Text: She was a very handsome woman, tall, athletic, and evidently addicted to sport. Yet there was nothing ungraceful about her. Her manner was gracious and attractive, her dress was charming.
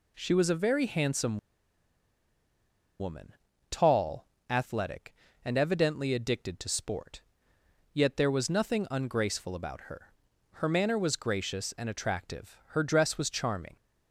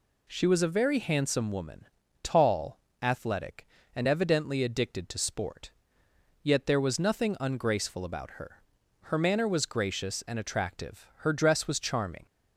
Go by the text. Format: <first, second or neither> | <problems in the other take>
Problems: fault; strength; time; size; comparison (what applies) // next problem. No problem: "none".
second | pauses between "handsome" and "woman"; strong; at 1.3 s; 1.6 s long